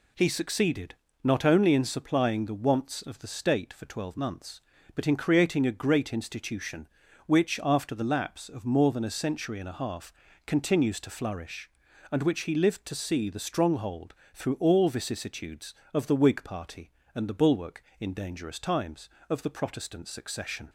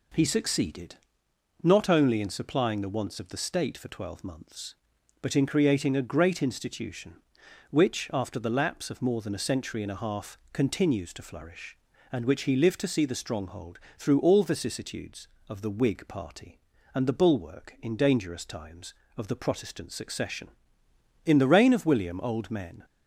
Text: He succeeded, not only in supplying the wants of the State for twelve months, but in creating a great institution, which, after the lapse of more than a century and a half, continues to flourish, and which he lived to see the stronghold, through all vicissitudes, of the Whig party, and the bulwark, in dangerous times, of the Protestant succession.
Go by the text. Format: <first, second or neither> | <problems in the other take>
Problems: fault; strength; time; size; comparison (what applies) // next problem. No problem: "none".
first | goes on to say "In the reign of William old men"; from 21.2 s on; 1.6 s long